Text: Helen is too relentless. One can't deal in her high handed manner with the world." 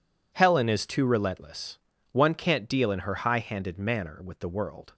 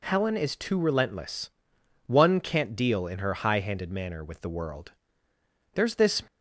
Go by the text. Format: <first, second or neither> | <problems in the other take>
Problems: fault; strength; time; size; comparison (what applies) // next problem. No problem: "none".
first | goes on to say "There's this"; slight; from 5.7 s on; 0.48 s long